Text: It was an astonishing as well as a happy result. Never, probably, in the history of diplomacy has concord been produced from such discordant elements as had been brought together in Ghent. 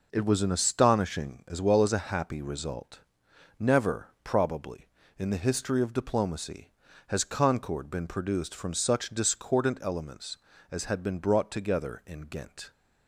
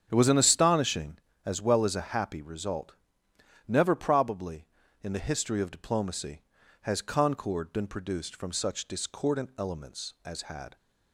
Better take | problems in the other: first | starts louder than the rest; strong; until 1.1 s; 8 dB // stops before "been brought together in Ghent"; at 10.7 s

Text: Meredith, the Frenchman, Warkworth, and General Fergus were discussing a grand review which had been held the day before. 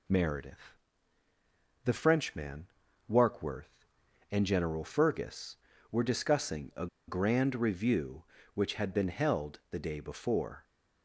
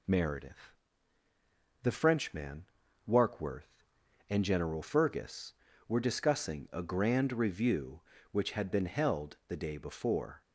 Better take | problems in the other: second | pauses between "a" and "grand"; slight; at 6.8 s; 0.21 s long

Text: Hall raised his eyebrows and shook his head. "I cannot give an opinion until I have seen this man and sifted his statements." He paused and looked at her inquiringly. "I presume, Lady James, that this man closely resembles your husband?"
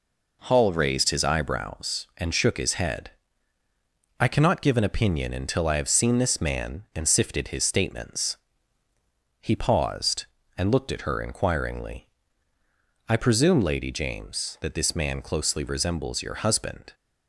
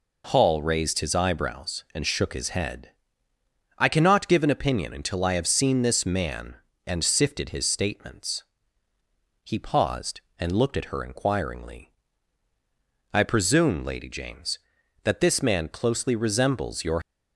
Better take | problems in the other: first | stops before "husband"; at 17.0 s

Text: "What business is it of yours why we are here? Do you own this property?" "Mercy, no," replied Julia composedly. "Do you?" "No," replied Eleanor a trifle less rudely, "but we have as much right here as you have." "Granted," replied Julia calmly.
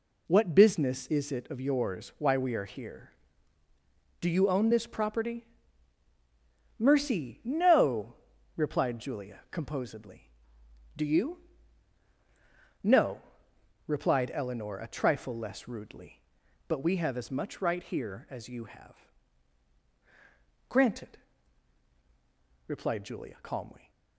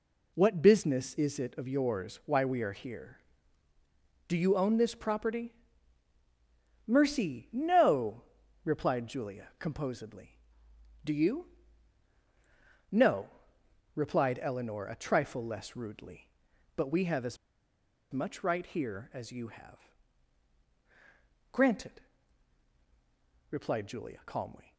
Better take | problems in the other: first | pauses between "as" and "much"; noticeable; at 17.3 s; 0.74 s long

